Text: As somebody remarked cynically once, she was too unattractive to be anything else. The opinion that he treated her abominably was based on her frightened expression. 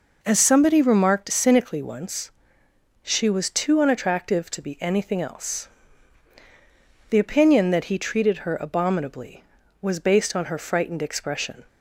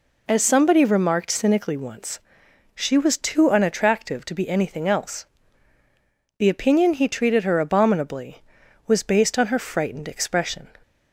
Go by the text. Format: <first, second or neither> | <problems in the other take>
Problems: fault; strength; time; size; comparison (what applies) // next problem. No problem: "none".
first | skips "that"; at 6.9 s